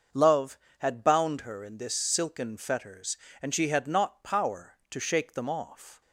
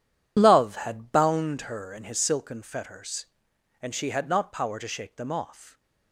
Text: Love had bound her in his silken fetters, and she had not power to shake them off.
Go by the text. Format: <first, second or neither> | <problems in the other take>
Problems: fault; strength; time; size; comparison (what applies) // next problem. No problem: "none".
second | starts louder than the rest; until 1.3 s; 6 dB // says "this" for "his"; at 1.7 s